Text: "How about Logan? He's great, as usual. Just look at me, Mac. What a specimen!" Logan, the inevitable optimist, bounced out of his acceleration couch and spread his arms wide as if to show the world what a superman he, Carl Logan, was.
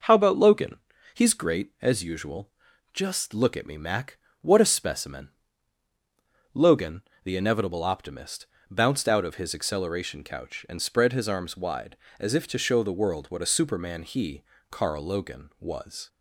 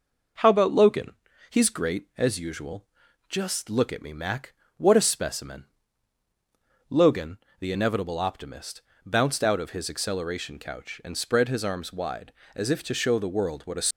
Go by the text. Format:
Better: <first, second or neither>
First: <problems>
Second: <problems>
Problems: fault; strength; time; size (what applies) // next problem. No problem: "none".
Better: first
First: none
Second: stops before "superman he Carl Logan was"; at 13.9 s